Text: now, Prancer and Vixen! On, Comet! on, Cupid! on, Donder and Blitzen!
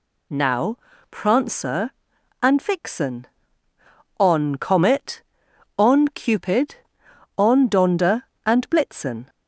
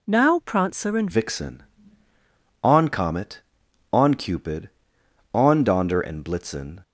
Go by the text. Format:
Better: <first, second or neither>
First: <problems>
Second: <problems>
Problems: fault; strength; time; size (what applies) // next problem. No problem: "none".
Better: first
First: none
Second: changes voice at "Vixen"; from 1.1 s on; 5.6 s long